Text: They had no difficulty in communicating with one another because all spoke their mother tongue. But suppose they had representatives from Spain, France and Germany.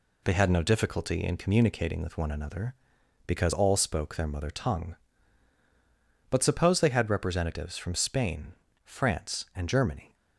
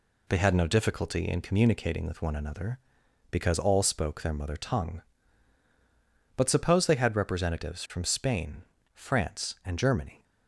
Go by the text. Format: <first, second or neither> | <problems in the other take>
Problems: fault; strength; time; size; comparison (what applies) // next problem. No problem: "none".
neither | none